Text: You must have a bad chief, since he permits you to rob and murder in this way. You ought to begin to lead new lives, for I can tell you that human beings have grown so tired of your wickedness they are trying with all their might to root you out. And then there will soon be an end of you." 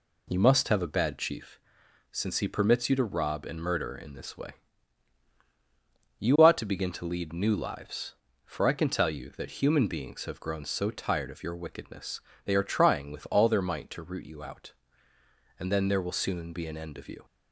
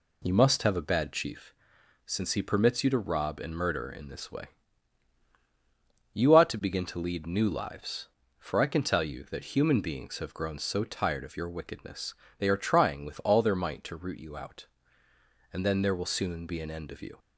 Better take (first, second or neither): neither